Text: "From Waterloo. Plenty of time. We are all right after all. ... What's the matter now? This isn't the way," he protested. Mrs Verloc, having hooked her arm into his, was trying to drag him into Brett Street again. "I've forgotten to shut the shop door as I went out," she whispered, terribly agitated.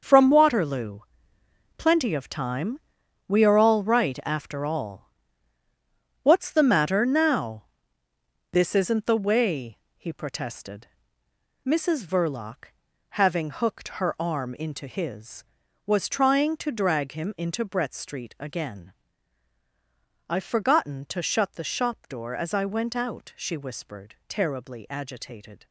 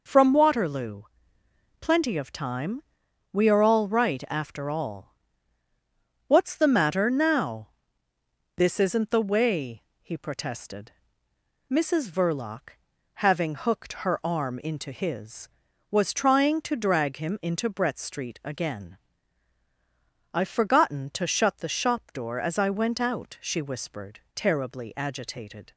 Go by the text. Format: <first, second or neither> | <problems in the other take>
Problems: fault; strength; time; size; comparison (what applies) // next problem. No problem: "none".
second | gets quieter; strong; throughout; 11 dB